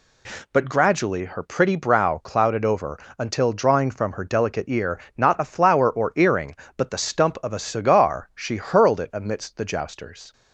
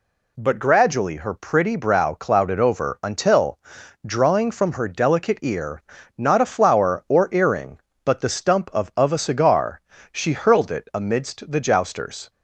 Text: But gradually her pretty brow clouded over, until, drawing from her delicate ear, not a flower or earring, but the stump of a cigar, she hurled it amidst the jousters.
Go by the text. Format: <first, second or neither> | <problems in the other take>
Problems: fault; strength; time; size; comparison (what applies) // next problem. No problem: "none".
first | says "of" twice; at 8.9 s